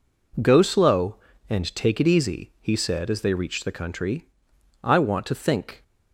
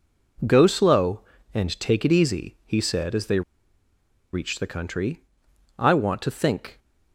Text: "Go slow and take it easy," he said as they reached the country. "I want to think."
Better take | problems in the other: first | pauses between "they" and "reached"; noticeable; at 3.4 s; 0.91 s long

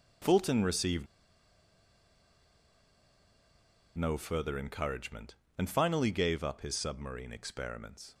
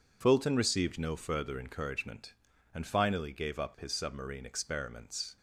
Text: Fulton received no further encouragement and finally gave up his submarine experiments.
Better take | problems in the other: second | pauses between "received" and "no"; strong; at 1.0 s; 2.9 s long

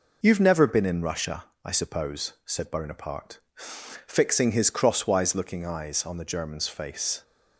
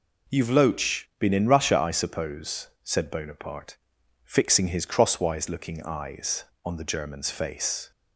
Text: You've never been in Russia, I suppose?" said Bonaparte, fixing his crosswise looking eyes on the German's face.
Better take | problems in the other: first | says "loach" for "never"; at 0.4 s

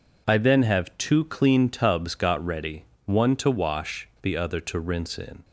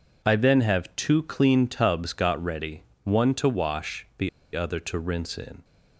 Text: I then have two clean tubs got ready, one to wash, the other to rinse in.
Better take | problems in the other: first | pauses between "the" and "other"; slight; at 4.2 s; 0.26 s long

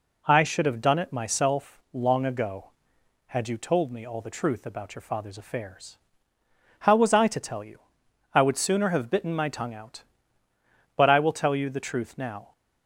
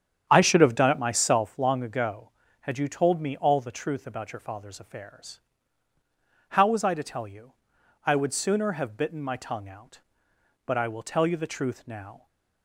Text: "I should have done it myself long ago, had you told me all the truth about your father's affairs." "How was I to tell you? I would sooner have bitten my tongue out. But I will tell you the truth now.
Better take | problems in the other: first | starts louder than the rest; strong; until 1.5 s; 8.5 dB

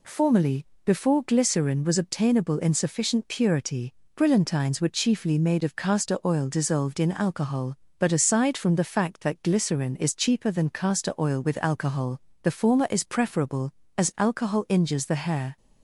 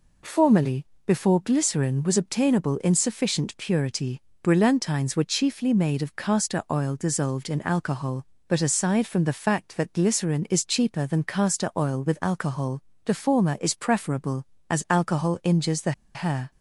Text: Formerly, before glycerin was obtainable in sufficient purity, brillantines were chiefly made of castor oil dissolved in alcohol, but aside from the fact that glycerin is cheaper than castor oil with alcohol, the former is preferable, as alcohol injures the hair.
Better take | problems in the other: first | pauses between "the" and "hair"; slight; at 15.9 s; 0.22 s long

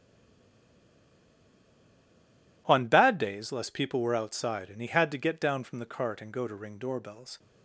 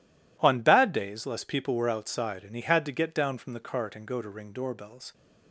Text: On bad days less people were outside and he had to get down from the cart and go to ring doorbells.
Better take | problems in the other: second | stays silent before the first word; strong; until 2.6 s; 2.6 s long

